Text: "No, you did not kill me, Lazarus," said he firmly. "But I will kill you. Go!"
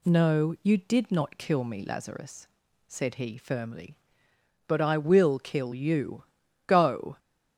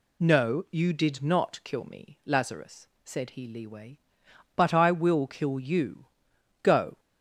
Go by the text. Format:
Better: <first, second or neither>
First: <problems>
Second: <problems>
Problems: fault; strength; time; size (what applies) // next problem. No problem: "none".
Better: first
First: none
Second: says "leeway" for "firmly"; at 3.4 s